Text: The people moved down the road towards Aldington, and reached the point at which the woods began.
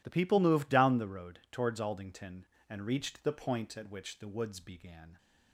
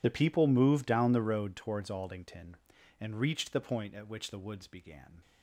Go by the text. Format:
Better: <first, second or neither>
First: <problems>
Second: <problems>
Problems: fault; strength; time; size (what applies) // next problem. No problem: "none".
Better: first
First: none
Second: loses the start of "The"; at 0.0 s; 30 ms